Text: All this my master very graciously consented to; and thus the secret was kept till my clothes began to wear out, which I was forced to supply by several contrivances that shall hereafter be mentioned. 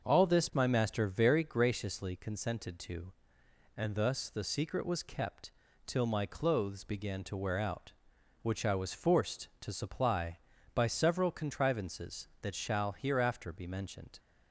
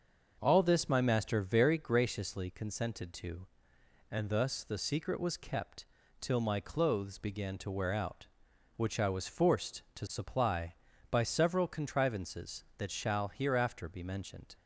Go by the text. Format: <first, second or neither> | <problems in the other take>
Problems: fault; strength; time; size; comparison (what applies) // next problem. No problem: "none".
neither | starts louder than the rest; the same in both // pauses between "kept" and "till"; slight; the same in both